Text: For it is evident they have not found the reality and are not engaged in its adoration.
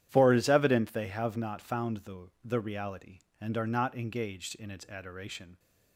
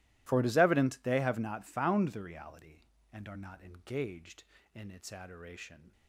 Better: second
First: starts louder than the rest; strong; until 1.1 s; 11 dB // says "the" twice; at 2.4 s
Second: none

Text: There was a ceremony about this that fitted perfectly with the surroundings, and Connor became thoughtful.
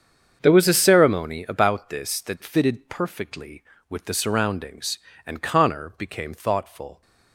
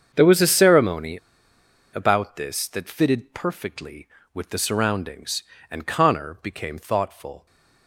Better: first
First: starts louder than the rest; strong; until 1.4 s; 7 dB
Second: starts louder than the rest; strong; until 1.1 s; 7 dB // pauses between "ceremony" and "about"; noticeable; at 1.1 s; 0.77 s long

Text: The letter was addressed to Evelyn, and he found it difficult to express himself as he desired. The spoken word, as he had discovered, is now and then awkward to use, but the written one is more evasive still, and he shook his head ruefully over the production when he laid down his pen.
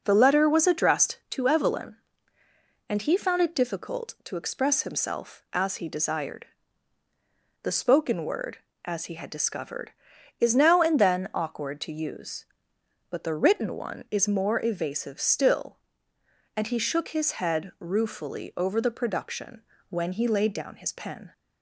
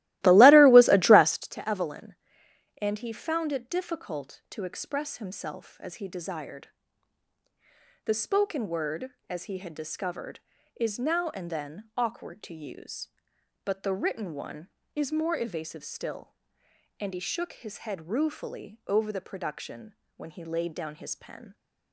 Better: first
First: pauses between "production" and "when"; slight; at 19.6 s; 0.28 s long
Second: starts louder than the rest; strong; until 1.5 s; 17.5 dB // pauses between "production" and "when"; slight; at 19.9 s; 0.24 s long

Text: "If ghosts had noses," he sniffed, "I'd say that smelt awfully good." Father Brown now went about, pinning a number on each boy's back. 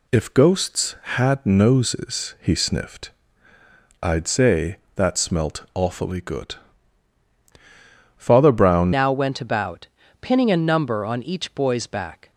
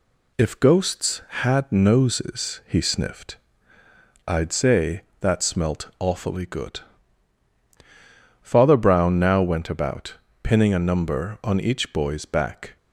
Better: second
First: changes voice at "now"; from 8.9 s on; 3.4 s long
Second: none

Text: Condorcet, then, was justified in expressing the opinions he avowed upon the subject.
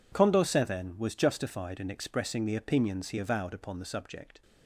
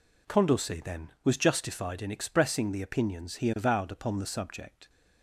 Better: neither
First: none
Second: none

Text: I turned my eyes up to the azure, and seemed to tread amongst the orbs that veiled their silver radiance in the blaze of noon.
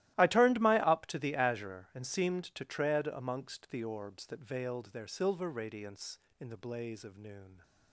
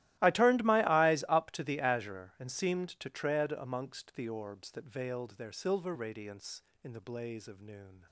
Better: second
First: starts louder than the rest; strong; until 1.1 s; 15.5 dB // skips "eyes"; at 0.8 s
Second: starts louder than the rest; strong; until 1.2 s; 16 dB

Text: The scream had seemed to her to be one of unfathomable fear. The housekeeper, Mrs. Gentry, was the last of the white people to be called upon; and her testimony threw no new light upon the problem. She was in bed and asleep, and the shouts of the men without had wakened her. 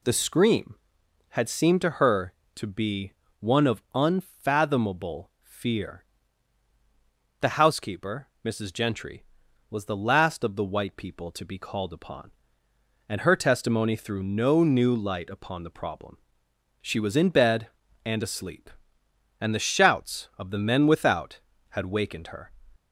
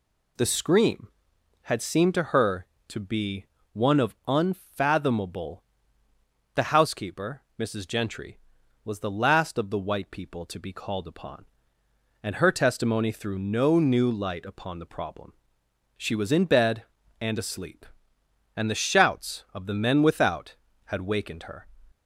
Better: first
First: pauses between "be" and "one"; slight; at 3.1 s; 0.26 s long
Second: pauses between "be" and "one"; slight; at 3.4 s; 0.26 s long // skips "fear"; at 6.0 s

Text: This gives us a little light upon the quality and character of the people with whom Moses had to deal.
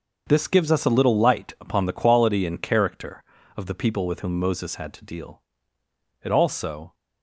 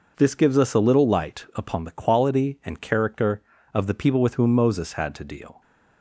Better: second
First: starts louder than the rest; until 1.2 s; 6 dB // goes on to say "It also"; noticeable; from 6.2 s on; 0.70 s long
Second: none

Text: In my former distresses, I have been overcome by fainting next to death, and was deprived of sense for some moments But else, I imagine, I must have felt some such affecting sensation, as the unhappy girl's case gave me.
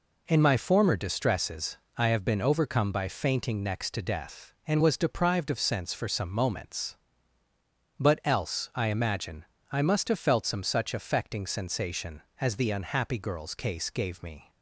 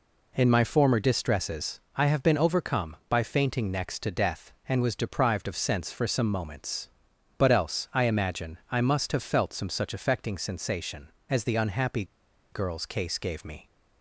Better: first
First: none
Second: pauses between "unhappy" and "girl's"; noticeable; at 12.0 s; 0.48 s long

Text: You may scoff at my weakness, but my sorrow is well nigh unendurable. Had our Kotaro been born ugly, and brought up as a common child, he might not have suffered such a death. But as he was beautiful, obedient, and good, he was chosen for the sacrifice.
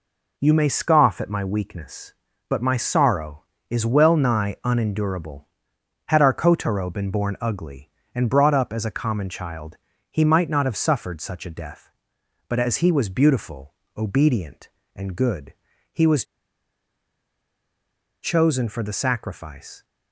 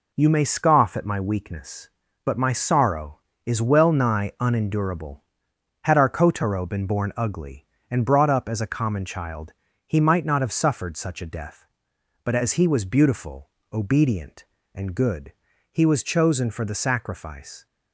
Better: second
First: pauses between "was" and "chosen"; strong; at 16.2 s; 1.9 s long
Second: none

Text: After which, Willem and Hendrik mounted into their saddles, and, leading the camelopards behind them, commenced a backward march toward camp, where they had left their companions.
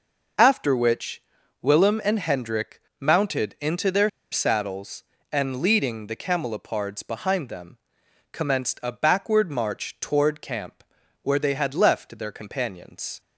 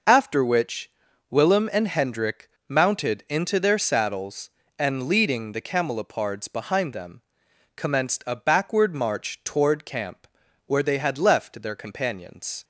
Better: second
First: pauses between "Hendrik" and "mounted"; slight; at 2.7 s; 0.20 s long // pauses between "their" and "saddles"; slight; at 4.0 s; 0.22 s long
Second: pauses between "Hendrik" and "mounted"; slight; at 2.4 s; 0.20 s long

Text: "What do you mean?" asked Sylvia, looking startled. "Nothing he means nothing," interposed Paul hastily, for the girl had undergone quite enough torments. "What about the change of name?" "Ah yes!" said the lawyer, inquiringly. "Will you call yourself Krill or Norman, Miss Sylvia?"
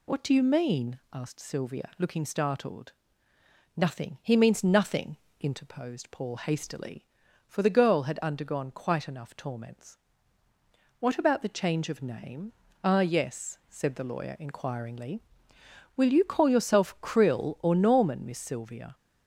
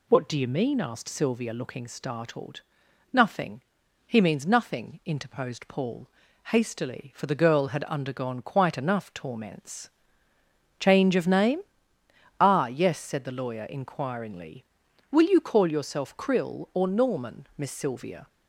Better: first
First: none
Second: pauses between "Nothing" and "he"; at 3.6 s; 0.44 s long // pauses between "Paul" and "hastily"; at 6.0 s; 0.38 s long // skips "What about the"; at 10.3 s

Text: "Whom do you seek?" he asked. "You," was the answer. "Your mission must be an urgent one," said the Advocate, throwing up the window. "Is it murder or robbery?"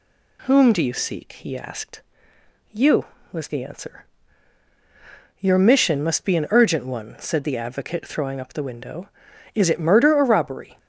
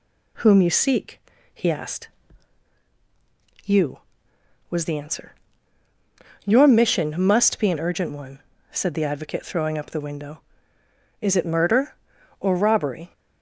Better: first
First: none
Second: skips "do"; at 0.6 s

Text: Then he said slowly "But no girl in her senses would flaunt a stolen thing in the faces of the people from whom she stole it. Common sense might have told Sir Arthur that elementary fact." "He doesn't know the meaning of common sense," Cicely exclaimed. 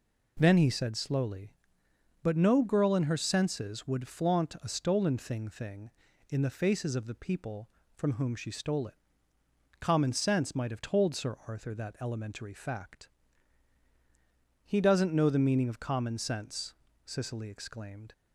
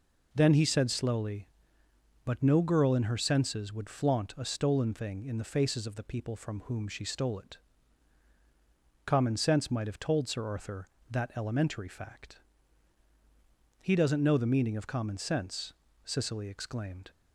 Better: second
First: says "thing" twice; at 5.4 s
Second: none

